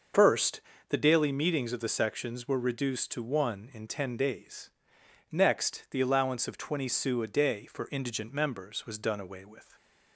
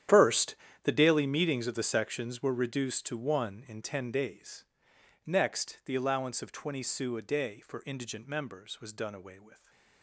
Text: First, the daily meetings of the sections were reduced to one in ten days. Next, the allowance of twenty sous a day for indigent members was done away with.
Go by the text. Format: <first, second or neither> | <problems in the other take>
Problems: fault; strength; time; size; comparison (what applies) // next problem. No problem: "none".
first | gets quieter; strong; throughout; 16.5 dB // starts louder than the rest; strong; until 1.4 s; 10.5 dB; also in the first